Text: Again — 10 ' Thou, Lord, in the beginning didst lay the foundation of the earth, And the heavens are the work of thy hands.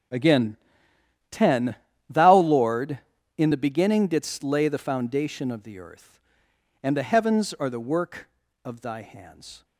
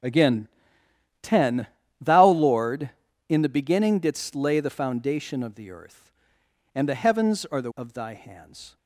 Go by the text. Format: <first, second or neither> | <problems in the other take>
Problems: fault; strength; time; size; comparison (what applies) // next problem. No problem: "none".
first | skips "work"; at 7.7 s